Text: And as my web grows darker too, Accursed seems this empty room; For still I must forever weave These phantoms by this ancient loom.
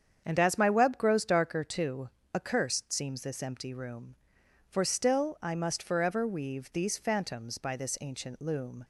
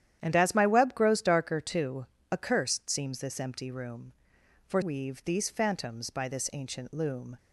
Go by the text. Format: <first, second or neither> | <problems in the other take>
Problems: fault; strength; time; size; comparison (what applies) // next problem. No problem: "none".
first | starts louder than the rest; strong; until 1.2 s; 10.5 dB; strong in the first // skips "still I must forever"; at 4.8 s